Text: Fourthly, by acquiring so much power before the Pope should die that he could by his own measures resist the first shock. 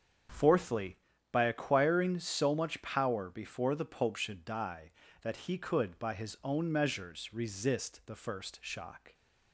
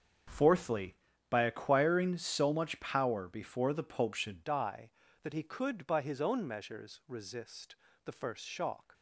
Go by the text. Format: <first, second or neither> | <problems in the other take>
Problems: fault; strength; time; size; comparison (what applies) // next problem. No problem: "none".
first | starts louder than the rest; until 1.6 s; 7 dB; strong in the first // changes voice at "die"; from 4.4 s on; 4.5 s long // pauses between "resist" and "the"; slight; at 7.7 s; 0.30 s long